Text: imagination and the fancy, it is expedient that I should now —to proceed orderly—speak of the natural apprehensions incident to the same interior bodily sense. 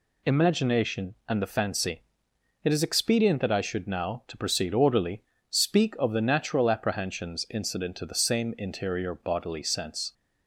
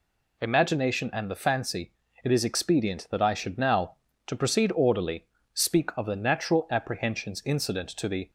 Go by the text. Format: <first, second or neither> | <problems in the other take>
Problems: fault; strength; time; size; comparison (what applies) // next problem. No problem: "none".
first | stops before "same interior bodily sense"; at 8.2 s